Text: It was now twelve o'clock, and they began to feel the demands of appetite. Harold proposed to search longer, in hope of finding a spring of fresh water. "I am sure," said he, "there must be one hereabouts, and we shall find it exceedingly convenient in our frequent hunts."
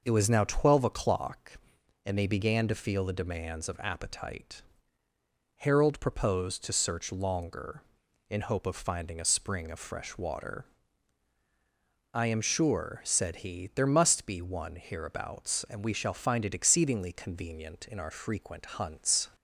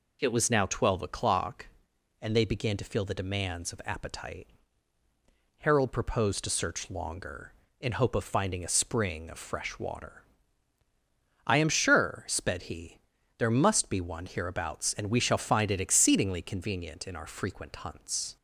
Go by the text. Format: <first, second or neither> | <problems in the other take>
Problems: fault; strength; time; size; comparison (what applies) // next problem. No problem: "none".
first | says "sped" for "said"; at 12.2 s